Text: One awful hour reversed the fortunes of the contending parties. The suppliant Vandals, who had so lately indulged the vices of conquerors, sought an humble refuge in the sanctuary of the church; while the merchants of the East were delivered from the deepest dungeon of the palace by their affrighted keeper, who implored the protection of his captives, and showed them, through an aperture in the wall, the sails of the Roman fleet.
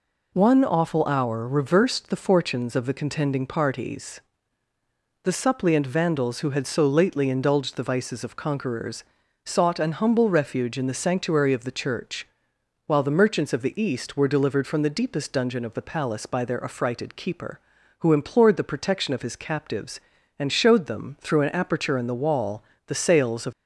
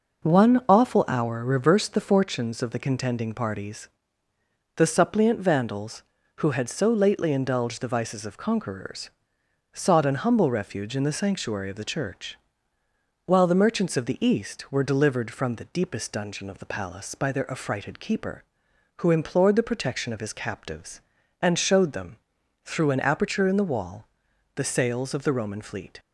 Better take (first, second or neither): second